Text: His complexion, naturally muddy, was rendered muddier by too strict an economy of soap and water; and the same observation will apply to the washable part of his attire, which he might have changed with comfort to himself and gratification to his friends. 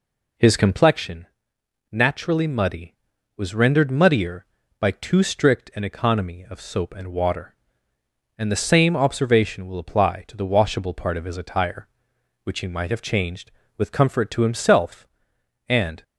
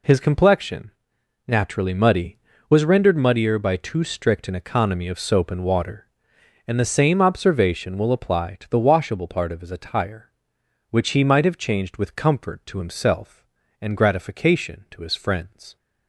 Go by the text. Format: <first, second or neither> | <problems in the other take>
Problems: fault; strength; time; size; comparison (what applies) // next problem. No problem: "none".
second | stops before "gratification to his friends"; at 16.0 s